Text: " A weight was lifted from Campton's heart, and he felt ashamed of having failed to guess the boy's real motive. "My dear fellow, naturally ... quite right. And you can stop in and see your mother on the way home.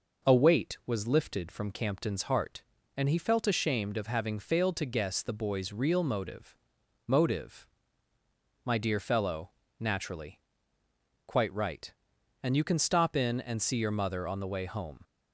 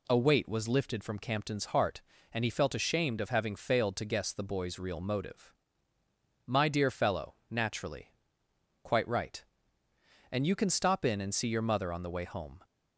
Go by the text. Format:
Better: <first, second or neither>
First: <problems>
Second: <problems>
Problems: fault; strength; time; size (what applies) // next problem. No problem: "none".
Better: second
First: says "motive" twice; at 7.0 s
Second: none